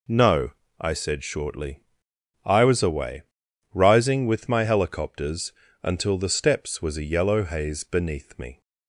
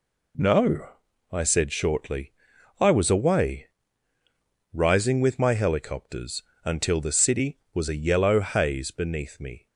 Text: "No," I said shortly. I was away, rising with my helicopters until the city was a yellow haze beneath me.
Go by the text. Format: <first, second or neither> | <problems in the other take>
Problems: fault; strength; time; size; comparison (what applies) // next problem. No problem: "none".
second | pauses between "helicopters" and "until"; slight; at 5.5 s; 0.30 s long; slight in the second // says "steps" for "city"; at 6.2 s